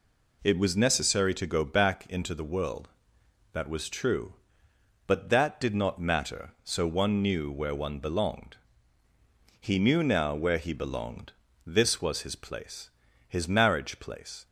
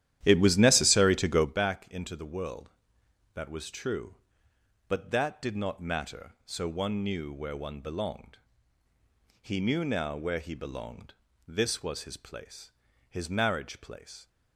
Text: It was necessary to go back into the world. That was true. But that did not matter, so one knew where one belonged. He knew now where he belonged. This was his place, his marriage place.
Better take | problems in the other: first | starts louder than the rest; strong; until 1.6 s; 12 dB

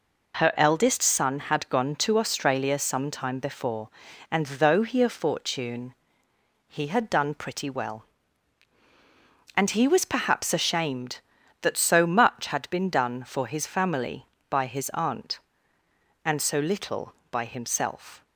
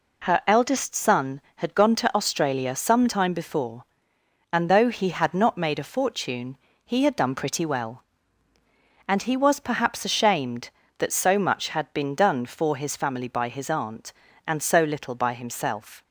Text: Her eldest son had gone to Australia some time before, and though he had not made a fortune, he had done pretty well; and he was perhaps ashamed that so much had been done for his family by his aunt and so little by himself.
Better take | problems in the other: second | skips "had not made"; at 5.0 s

